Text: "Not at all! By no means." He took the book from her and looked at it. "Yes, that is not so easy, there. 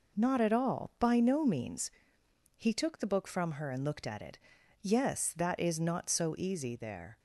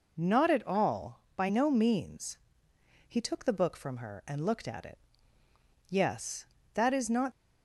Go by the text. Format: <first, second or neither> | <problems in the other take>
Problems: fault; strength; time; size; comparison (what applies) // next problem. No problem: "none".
first | stops before "so easy there"; at 7.3 s